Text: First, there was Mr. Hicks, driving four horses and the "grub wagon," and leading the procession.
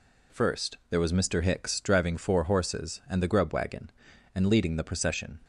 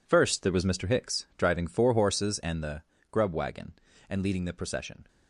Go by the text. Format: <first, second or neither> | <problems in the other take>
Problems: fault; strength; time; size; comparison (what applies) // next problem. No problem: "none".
first | gets quieter; strong; throughout; 13 dB // pauses between "the" and "grub"; slight; at 2.8 s; 0.26 s long